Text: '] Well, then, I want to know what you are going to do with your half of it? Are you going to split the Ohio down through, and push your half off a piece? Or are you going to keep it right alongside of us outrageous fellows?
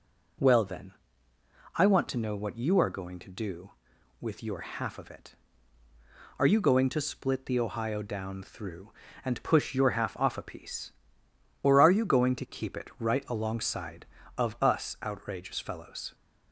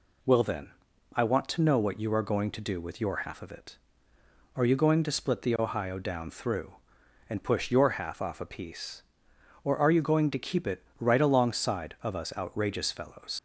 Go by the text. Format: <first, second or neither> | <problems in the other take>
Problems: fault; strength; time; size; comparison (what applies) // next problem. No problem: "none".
first | pauses between "it" and "right"; slight; at 10.8 s; 0.16 s long // leaves "fellows" unfinished; at 13.3 s; 55 ms